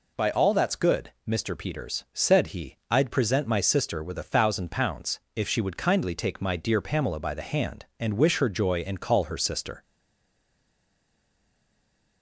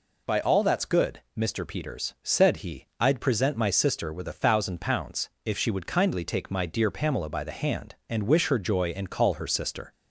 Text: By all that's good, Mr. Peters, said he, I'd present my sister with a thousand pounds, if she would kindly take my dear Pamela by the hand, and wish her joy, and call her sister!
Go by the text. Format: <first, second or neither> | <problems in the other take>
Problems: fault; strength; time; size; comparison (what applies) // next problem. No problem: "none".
second | stays silent after the last word; from 9.8 s on; 2.4 s long